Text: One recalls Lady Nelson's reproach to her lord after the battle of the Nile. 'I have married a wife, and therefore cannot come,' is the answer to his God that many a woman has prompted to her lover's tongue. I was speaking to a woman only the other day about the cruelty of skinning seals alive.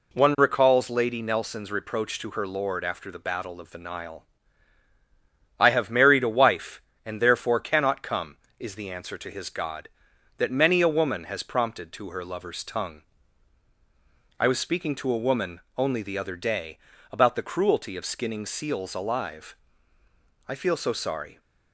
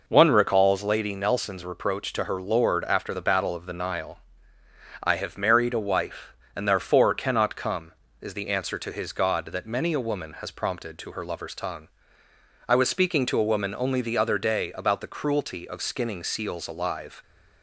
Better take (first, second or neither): second